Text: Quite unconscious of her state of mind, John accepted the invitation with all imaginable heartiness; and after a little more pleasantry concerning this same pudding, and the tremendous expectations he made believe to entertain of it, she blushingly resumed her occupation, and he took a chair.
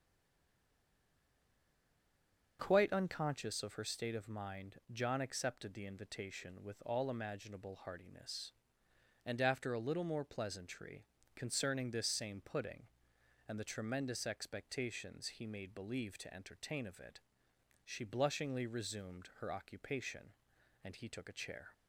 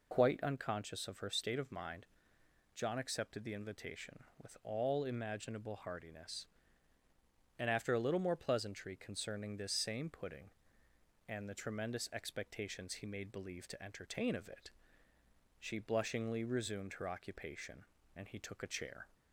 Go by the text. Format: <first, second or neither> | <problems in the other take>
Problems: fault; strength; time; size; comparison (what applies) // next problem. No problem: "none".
second | stays silent before the first word; strong; until 2.5 s; 2.5 s long // starts louder than the rest; until 3.6 s; 6.5 dB // pauses between "pleasantry" and "concerning"; slight; at 11.0 s; 0.28 s long